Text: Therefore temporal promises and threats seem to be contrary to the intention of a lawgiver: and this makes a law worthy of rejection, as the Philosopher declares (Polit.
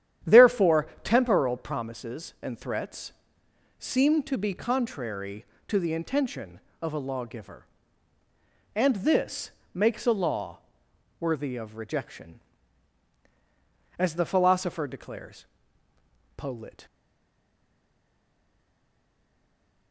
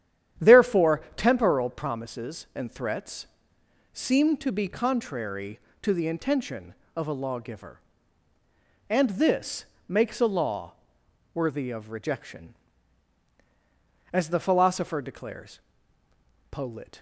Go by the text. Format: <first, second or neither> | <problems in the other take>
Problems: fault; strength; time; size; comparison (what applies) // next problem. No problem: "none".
second | starts louder than the rest; strong; until 1.4 s; 10 dB; strong in the second // pauses between "Therefore" and "temporal"; slight; at 0.8 s; 0.16 s long // pauses between "threats" and "seem"; noticeable; at 3.1 s; 0.68 s long; noticeable in the second // pauses between "this" and "makes"; slight; at 9.4 s; 0.24 s long; slight in the second // pauses between "law" and "worthy"; noticeable; at 10.5 s; 0.60 s long; noticeable in the second // stays silent after the last word; strong; from 16.8 s on; 3.1 s long